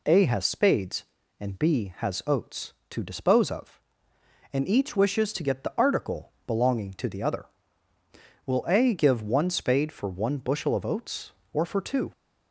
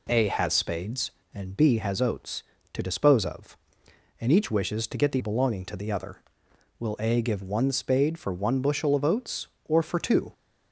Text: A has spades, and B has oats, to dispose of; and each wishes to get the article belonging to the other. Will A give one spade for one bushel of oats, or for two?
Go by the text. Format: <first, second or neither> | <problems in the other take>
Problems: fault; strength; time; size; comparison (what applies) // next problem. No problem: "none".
first | skips "article"; at 5.1 s